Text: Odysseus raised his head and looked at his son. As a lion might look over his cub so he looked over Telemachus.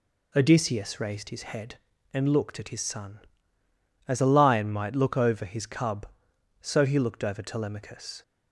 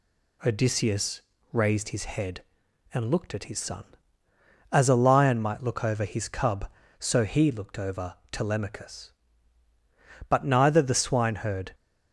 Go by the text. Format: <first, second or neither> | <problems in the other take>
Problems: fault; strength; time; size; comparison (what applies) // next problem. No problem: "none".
first | pauses between "Odysseus" and "raised"; slight; at 1.2 s; 0.32 s long // pauses between "over" and "Telemachus"; slight; at 8.1 s; 0.16 s long // goes on to say "But neither the swineherd"; from 10.2 s on; 1.4 s long